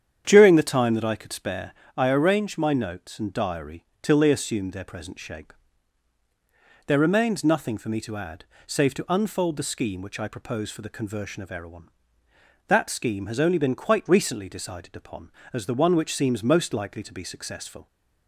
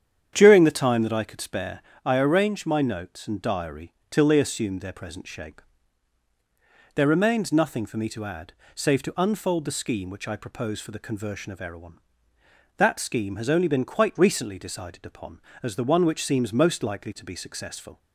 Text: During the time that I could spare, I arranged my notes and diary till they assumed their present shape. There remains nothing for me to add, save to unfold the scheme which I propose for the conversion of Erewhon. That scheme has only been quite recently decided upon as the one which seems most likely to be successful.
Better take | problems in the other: neither | starts louder than the rest; strong; the same in both // pauses between "diary" and "till"; slight; the same in both

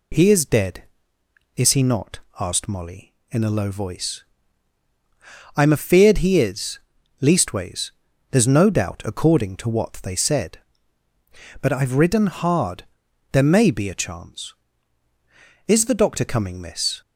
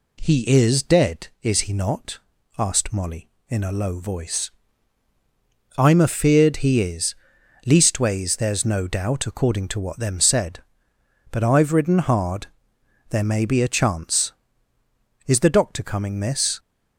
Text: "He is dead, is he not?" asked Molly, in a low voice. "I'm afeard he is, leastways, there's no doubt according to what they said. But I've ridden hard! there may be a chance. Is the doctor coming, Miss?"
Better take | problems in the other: first | says "them" for "they"; at 9.9 s

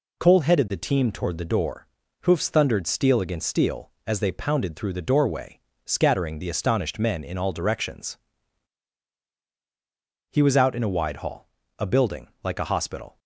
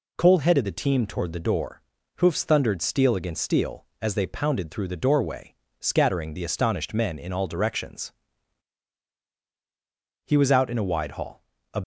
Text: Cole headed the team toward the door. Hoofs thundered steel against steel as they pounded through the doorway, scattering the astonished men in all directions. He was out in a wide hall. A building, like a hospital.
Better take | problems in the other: first | stops before "building like a hospital"; at 11.8 s

